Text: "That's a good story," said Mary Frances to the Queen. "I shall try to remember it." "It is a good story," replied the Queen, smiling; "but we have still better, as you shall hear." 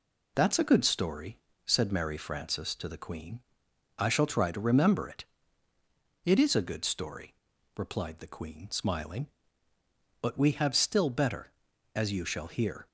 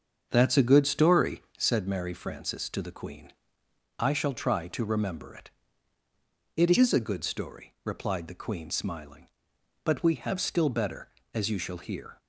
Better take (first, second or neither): first